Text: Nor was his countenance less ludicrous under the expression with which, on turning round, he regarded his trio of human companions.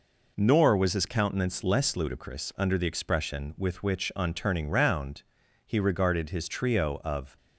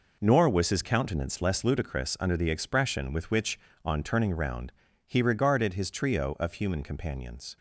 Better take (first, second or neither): second